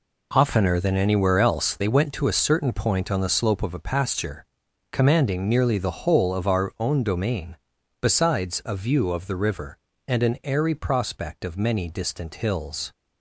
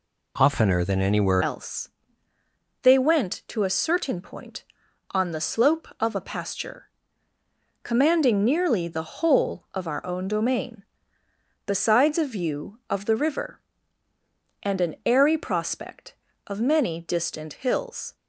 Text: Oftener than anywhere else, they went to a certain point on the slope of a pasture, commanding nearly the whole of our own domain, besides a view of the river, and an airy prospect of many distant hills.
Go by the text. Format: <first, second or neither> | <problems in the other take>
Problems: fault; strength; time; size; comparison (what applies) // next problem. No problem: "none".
first | changes voice at "else"; from 1.4 s on; 16.7 s long